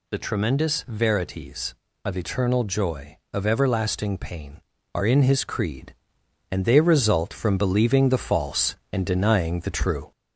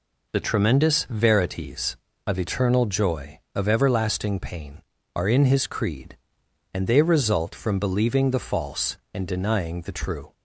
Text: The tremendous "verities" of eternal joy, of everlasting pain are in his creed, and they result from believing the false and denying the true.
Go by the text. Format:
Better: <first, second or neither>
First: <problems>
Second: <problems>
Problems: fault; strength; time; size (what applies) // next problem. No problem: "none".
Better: second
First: gets louder; slight; throughout; 3 dB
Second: none